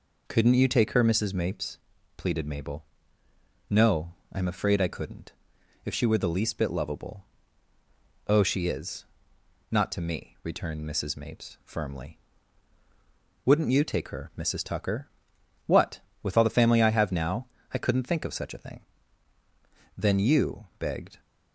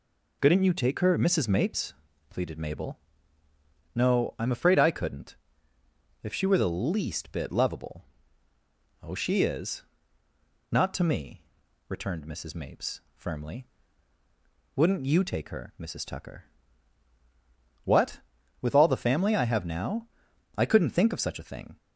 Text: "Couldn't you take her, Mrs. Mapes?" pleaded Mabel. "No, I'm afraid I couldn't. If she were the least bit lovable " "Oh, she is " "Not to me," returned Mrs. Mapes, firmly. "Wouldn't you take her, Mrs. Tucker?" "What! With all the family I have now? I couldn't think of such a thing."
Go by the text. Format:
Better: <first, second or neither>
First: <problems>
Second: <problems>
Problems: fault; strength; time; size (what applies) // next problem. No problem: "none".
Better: second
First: goes on to say "Then you begged"; noticeable; from 19.9 s on; 1.2 s long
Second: none